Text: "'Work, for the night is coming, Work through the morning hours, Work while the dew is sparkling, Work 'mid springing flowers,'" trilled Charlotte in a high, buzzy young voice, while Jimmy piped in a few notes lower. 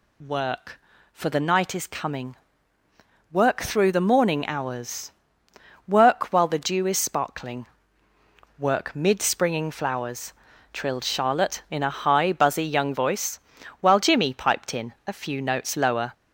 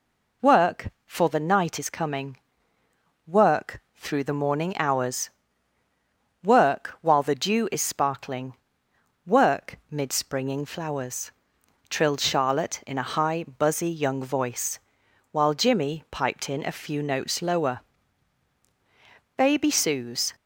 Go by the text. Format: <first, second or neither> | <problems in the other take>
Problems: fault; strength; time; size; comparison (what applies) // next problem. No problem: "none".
first | pauses between "Work" and "through"; slight; at 3.7 s; 0.16 s long // goes on to say "Baby Sue's"; noticeable; from 19.3 s on; 0.98 s long